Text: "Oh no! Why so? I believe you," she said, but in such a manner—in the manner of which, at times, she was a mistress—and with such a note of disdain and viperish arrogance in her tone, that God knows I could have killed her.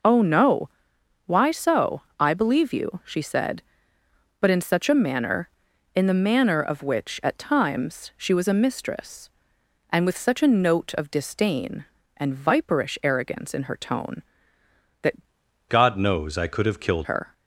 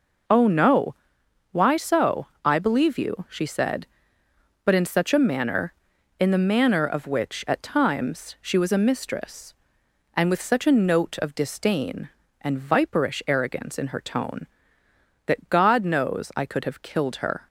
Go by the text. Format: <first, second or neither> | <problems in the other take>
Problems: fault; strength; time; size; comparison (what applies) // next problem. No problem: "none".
second | changes voice from "God" to "killed"; from 15.6 to 17.0 s; 1.4 s long